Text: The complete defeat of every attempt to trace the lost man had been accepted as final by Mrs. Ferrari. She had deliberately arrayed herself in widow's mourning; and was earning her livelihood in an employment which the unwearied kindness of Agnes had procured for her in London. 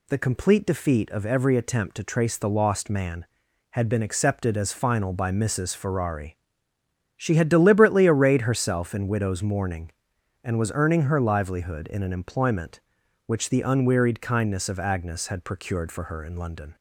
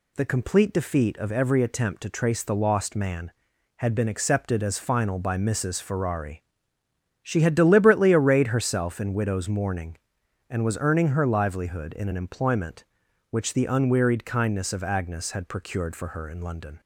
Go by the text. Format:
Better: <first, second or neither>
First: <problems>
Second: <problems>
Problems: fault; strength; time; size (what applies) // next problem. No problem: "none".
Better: neither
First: none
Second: none